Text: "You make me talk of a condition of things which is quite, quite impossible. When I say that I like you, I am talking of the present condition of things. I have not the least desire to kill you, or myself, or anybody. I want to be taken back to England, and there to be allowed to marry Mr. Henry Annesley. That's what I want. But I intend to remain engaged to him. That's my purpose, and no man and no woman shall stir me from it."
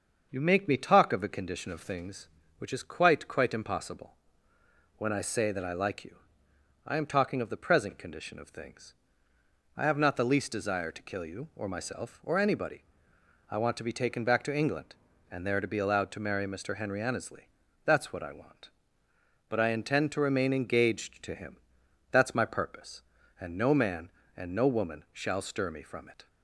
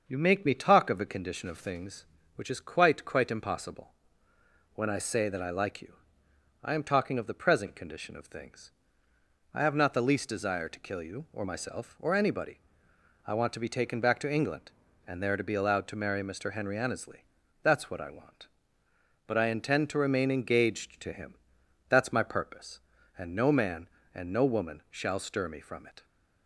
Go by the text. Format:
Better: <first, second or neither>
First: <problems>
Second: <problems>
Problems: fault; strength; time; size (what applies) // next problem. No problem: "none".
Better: neither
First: starts louder than the rest; until 1.3 s; 6.5 dB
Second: starts louder than the rest; until 1.0 s; 6.5 dB